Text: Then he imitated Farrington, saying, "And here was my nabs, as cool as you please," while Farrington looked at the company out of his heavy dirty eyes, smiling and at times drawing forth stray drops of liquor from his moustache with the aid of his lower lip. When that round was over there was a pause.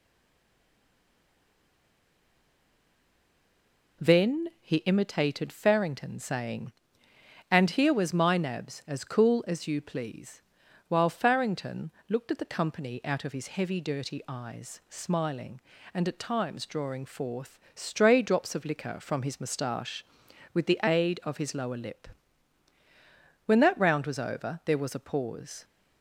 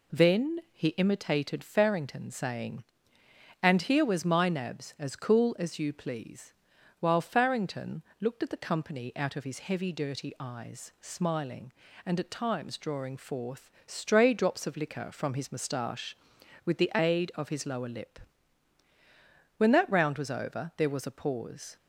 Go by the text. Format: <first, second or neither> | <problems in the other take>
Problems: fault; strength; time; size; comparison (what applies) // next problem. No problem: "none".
second | stays silent before the first word; strong; until 4.0 s; 4.0 s long // pauses between "Farrington" and "looked"; slight; at 11.9 s; 0.18 s long; slight in the second // pauses between "forth" and "stray"; slight; at 17.5 s; 0.16 s long; slight in the second